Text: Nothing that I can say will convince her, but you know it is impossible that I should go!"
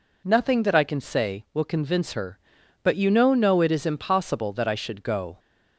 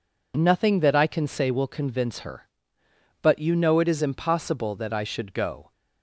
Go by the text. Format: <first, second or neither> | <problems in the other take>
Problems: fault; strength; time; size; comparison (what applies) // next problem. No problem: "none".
second | says "know" twice; at 3.3 s